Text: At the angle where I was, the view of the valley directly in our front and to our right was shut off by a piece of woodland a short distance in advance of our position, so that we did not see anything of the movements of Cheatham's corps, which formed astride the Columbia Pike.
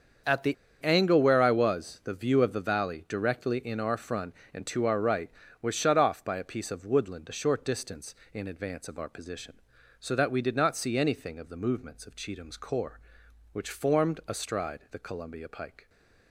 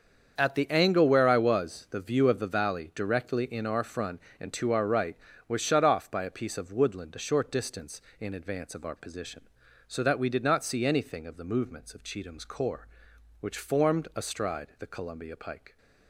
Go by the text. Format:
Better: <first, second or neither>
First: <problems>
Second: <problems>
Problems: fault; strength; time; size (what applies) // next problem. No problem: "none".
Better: second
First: starts louder than the rest; until 1.5 s; 7 dB // pauses between "the" and "angle"; slight; at 0.5 s; 0.28 s long // stays silent after the last word; slight; from 15.7 s on; 0.6 s long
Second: starts louder than the rest; until 1.3 s; 7 dB